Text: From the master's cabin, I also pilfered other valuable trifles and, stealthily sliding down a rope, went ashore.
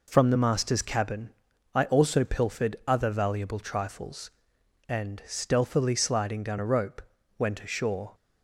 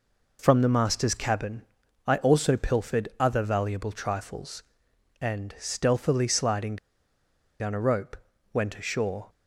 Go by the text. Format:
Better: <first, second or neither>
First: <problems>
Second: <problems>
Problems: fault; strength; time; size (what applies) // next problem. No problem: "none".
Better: first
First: none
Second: pauses between "sliding" and "down"; noticeable; at 6.7 s; 0.83 s long